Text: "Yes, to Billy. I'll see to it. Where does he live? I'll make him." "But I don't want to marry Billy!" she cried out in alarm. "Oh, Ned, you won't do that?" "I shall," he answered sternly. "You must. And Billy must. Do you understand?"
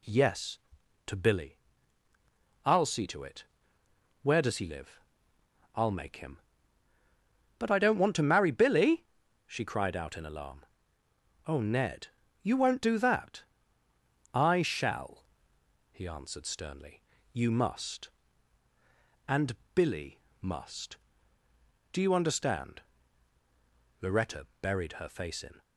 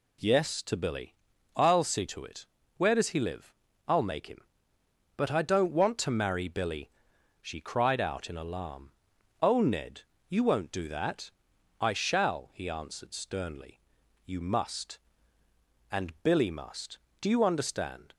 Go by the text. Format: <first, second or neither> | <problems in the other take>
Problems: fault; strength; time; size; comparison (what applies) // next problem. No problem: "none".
second | pauses between "And" and "Billy"; slight; at 19.5 s; 0.18 s long // pauses between "Billy" and "must"; slight; at 20.1 s; 0.22 s long // goes on to say "Loretta buried her face in"; from 24.0 s on; 1.6 s long